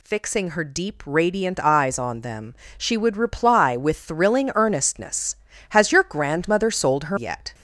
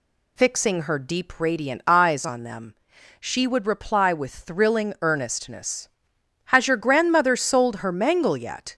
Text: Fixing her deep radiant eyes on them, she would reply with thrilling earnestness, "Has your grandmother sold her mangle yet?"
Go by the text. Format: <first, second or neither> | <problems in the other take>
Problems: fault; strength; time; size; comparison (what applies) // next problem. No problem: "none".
second | skips "mangle"; at 7.1 s